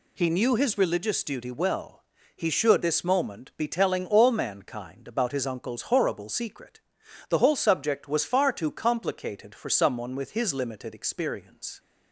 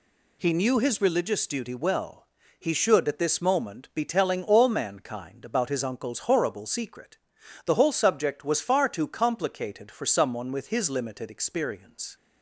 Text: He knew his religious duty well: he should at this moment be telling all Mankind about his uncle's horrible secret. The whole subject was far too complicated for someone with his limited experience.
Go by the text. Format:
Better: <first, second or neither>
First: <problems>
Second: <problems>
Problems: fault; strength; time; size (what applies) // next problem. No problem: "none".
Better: second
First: skips "at"; at 2.8 s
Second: none